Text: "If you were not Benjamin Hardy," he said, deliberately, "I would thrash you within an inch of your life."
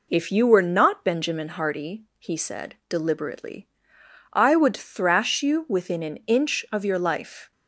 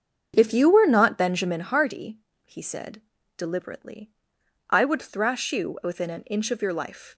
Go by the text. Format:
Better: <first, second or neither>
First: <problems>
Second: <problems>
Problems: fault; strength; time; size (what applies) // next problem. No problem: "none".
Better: first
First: none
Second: starts louder than the rest; until 1.8 s; 7 dB